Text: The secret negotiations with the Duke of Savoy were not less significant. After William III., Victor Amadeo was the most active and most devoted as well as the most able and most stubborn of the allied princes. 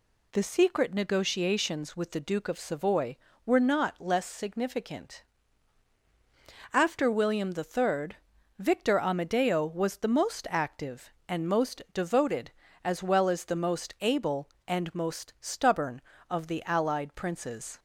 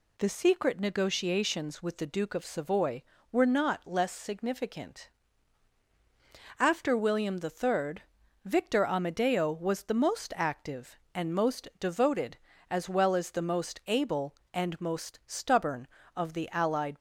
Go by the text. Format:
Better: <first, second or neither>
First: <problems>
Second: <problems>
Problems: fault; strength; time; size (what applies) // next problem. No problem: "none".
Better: first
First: none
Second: stops before "princes"; at 16.9 s